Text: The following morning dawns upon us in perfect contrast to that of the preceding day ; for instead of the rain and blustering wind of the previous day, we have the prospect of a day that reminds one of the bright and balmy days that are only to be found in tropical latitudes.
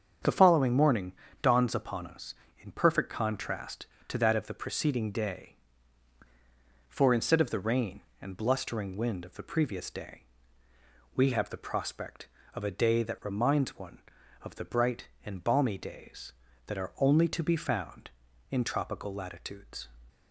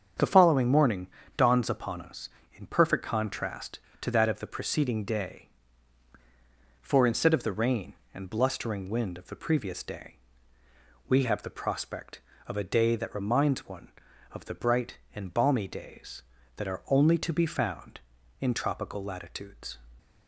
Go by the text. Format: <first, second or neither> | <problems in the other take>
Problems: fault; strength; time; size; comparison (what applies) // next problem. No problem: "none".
neither | starts louder than the rest; strong; the same in both // pauses between "morning" and "dawns"; slight; the same in both